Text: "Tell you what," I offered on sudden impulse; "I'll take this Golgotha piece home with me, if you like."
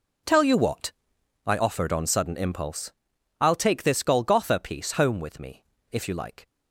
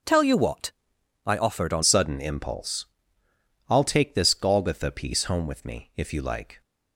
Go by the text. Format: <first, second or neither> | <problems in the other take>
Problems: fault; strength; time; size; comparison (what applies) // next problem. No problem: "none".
first | starts louder than the rest; noticeable; until 1.5 s; 6 dB // changes voice at "sudden"; from 1.8 s on; 4.8 s long